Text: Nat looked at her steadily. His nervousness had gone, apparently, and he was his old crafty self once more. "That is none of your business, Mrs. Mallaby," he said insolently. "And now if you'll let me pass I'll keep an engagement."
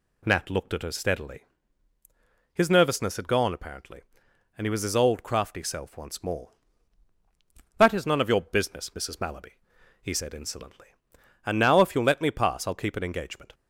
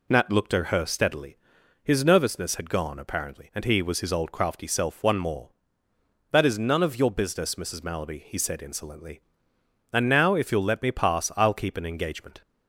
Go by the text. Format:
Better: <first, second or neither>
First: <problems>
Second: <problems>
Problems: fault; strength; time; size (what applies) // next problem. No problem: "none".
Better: first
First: none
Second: says "one" for "once"; at 5.0 s